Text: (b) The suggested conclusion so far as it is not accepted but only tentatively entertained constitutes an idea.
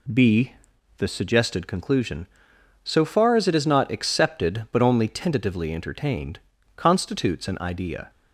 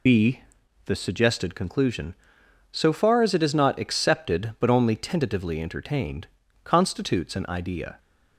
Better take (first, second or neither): first